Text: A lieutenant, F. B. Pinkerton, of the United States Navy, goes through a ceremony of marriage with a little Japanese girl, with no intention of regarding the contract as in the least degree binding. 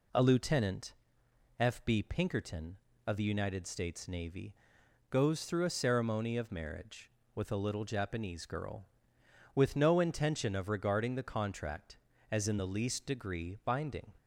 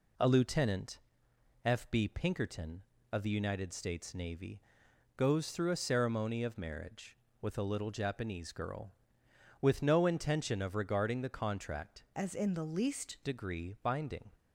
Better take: first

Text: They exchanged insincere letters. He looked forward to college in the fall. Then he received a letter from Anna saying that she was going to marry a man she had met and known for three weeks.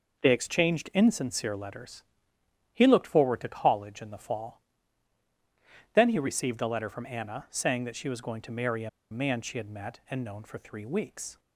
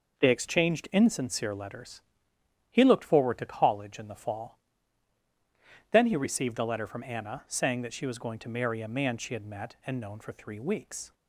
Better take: second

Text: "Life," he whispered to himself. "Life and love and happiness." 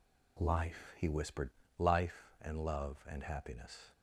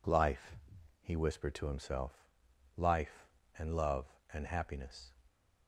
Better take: second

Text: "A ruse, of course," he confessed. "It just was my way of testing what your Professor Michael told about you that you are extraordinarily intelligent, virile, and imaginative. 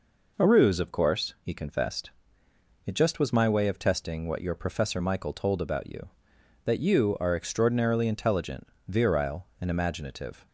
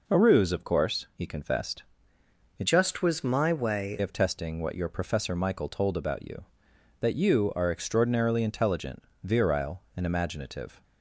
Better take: first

